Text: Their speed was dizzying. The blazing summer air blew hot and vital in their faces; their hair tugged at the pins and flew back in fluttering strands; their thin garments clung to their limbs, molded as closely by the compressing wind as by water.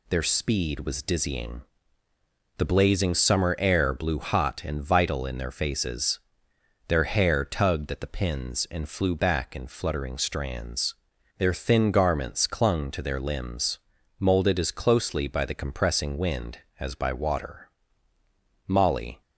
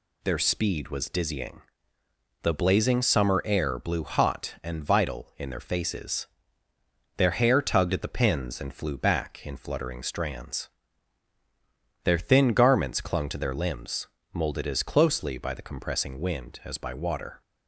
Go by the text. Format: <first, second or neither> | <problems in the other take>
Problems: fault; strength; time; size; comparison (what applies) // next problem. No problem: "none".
second | goes on to say "Molly"; from 18.6 s on; 0.54 s long